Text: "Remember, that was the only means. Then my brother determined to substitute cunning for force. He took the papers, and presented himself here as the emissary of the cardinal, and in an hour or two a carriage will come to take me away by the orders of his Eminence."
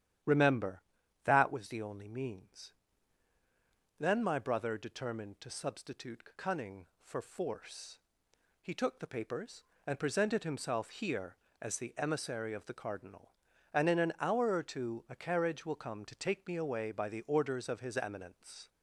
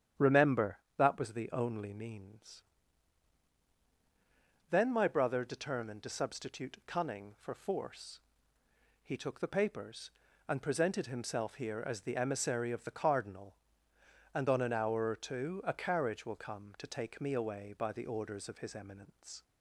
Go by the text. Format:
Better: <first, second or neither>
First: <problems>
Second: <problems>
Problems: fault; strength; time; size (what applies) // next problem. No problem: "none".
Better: first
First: starts louder than the rest; strong; until 1.6 s; 10.5 dB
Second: starts louder than the rest; strong; until 1.3 s; 9.5 dB // says "on" for "in"; at 14.4 s